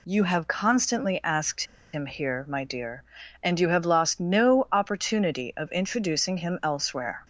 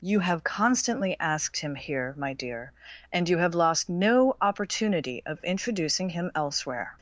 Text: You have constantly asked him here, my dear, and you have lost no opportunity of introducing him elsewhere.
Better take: second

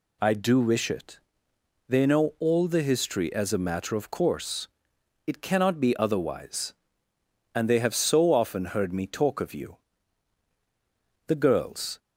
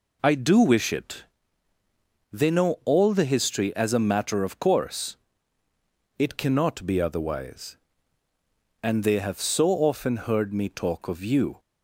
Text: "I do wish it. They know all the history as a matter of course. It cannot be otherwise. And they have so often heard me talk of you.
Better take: second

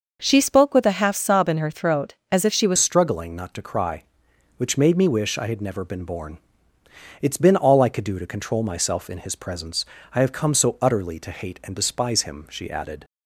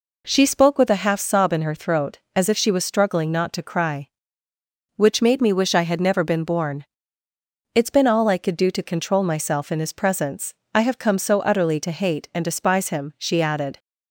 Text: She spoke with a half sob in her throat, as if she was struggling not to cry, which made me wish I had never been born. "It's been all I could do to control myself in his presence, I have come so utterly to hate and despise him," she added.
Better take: second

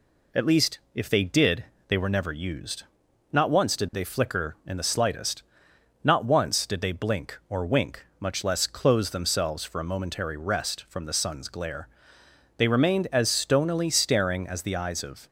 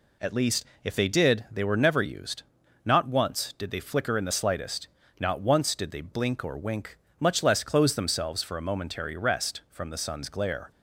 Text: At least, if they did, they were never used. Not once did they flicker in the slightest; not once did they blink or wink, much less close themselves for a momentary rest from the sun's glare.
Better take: second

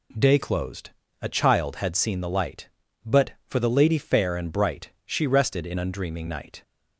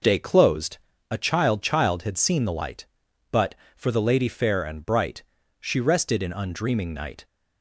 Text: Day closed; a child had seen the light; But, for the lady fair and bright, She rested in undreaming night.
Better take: first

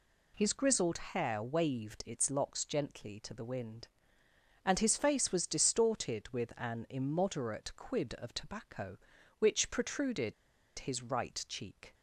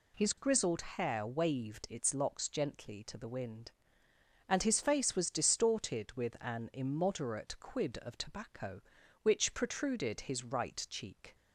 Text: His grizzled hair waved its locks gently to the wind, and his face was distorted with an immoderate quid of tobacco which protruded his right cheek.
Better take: second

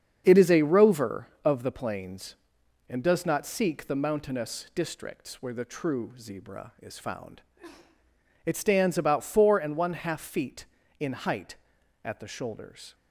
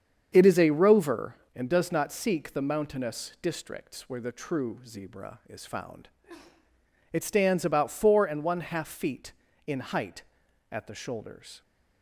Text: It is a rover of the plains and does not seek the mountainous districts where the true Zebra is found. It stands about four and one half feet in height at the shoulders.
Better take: first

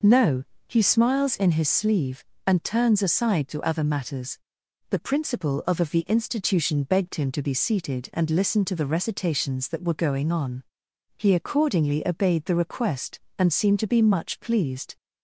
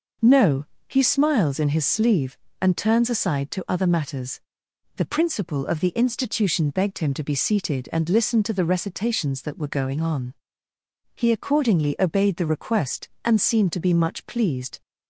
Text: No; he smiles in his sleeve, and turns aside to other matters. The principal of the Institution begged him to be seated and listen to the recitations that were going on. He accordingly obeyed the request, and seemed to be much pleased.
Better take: second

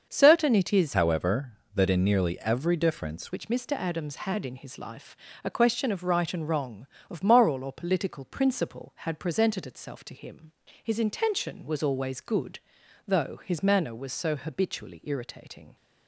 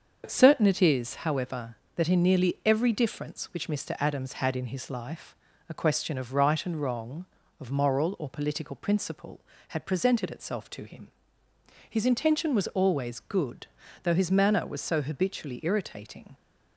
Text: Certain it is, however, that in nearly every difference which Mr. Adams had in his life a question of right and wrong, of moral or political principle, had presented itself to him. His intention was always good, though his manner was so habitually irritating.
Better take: second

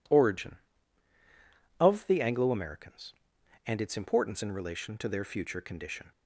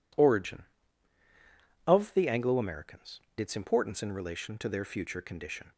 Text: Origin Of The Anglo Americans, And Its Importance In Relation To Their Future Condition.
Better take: first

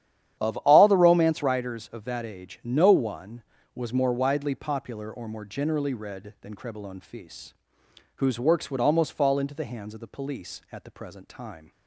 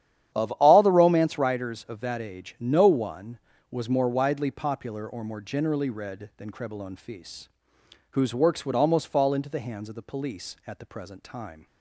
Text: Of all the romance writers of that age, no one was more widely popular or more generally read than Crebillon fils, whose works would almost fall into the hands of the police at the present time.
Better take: neither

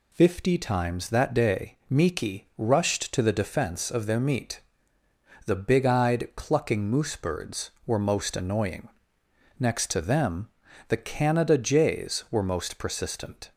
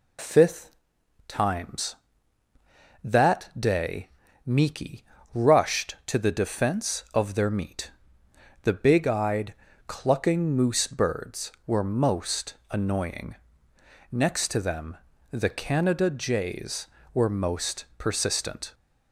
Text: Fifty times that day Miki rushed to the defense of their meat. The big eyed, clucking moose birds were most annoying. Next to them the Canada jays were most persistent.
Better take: first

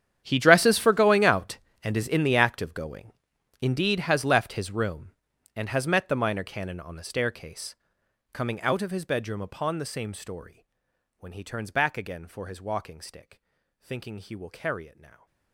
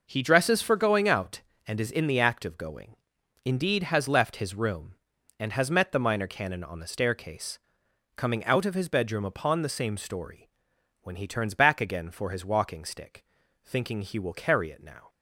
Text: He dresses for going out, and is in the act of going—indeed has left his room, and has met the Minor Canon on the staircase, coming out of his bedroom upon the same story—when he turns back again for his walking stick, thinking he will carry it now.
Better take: second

